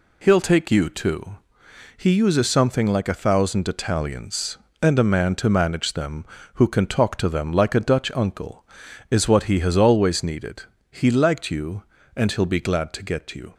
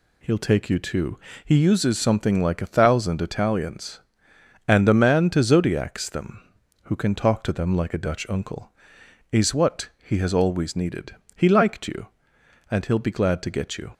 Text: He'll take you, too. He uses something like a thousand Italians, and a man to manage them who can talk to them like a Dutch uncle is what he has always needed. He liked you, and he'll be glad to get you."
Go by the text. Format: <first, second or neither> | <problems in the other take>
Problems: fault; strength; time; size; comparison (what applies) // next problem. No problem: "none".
first | says "zodiacs" for "manage"; at 5.4 s // pauses between "what" and "he"; slight; at 9.8 s; 0.16 s long